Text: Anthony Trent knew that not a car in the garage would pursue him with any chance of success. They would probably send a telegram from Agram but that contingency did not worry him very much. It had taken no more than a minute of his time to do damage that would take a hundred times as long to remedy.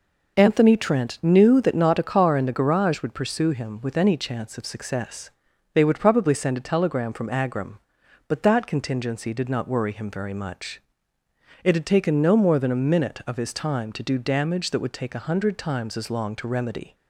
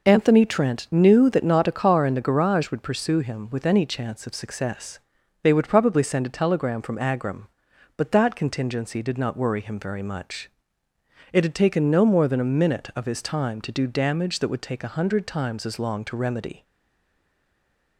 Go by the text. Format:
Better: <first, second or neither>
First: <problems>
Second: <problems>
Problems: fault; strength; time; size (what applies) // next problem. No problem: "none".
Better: first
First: none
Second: stays silent after the last word; noticeable; from 16.6 s on; 1.3 s long